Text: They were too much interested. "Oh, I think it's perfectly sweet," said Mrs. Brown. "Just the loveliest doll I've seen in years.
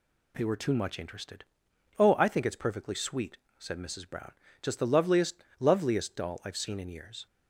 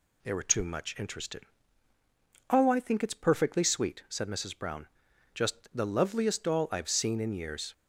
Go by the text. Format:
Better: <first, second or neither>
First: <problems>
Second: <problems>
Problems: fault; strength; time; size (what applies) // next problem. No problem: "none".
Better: second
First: says "loveliest" twice; at 5.5 s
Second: none